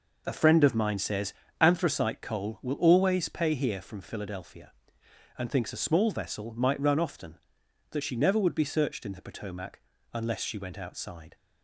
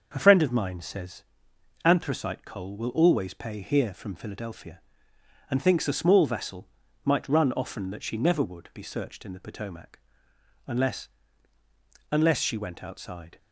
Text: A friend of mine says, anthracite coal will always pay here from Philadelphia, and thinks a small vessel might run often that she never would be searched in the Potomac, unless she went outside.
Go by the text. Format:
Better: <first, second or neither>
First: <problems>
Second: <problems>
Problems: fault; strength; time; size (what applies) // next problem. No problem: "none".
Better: first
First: none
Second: starts louder than the rest; until 1.1 s; 6.5 dB // pauses between "vessel" and "might"; slight; at 6.6 s; 0.34 s long // says "unless" twice; at 12.1 s